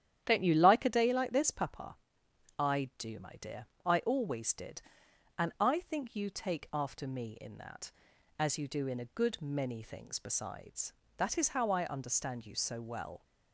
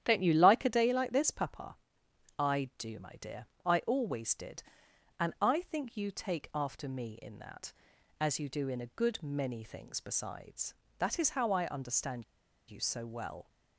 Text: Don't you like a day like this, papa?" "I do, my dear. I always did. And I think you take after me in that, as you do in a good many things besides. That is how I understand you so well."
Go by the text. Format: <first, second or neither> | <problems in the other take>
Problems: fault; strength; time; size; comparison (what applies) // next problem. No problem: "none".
first | starts louder than the rest; strong; until 1.0 s; 10.5 dB; strong in the first // pauses between "understand" and "you"; at 12.2 s; 0.44 s long